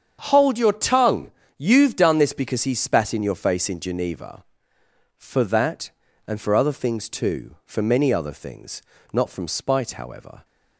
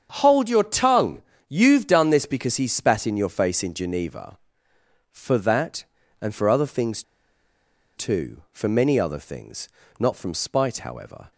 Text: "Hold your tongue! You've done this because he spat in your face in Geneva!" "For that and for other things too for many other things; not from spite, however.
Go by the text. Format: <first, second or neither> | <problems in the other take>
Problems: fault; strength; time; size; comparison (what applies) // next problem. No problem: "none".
first | starts louder than the rest; strong; until 1.4 s; 7.5 dB; strong in the first // pauses between "things" and "too"; noticeable; at 7.0 s; 0.94 s long